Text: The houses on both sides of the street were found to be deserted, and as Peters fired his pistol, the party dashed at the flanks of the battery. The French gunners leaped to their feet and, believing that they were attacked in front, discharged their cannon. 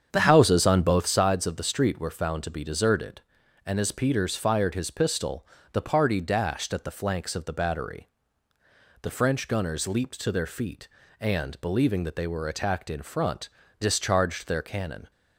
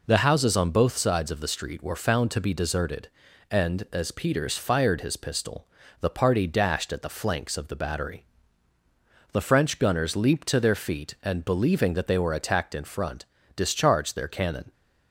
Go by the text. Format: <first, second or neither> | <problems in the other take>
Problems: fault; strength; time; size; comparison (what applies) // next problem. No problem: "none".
second | starts louder than the rest; strong; until 1.3 s; 8 dB